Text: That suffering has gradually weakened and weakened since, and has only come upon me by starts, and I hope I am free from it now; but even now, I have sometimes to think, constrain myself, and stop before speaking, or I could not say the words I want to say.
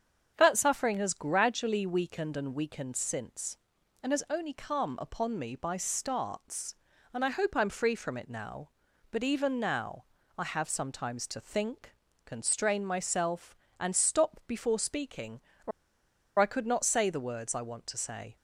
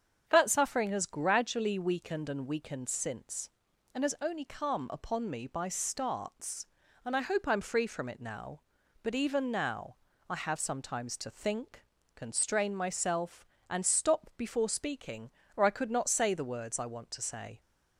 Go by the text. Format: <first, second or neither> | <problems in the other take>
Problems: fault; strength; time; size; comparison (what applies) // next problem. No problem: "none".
second | starts louder than the rest; strong; until 1.3 s; 7.5 dB; strong in the second // pauses between "or" and "I"; noticeable; at 15.7 s; 0.70 s long